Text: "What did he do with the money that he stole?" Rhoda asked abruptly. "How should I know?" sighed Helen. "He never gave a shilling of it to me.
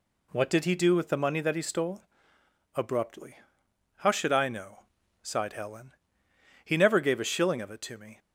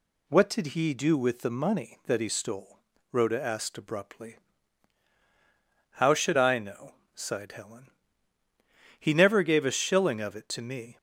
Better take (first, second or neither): second